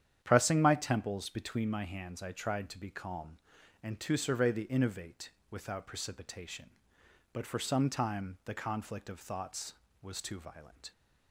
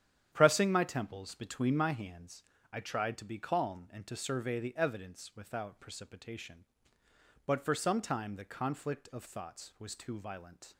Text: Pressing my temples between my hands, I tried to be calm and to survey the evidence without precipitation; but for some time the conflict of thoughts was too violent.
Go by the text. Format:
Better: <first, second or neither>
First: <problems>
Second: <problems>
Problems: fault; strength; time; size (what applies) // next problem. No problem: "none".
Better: second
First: starts louder than the rest; strong; until 1.2 s; 9.5 dB // says "innovate" for "evidence"; at 4.6 s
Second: starts louder than the rest; strong; until 1.3 s; 9.5 dB